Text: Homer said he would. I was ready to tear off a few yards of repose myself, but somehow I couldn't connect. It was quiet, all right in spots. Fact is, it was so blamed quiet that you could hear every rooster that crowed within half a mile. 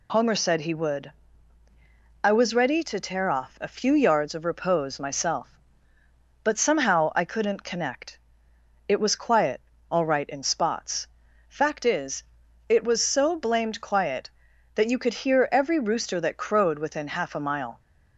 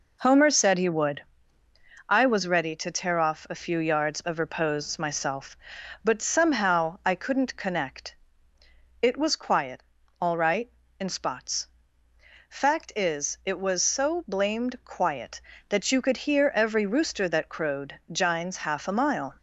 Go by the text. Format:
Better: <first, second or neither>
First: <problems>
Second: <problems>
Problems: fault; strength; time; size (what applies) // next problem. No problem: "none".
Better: first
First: none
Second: says "jines" for "within"; at 18.1 s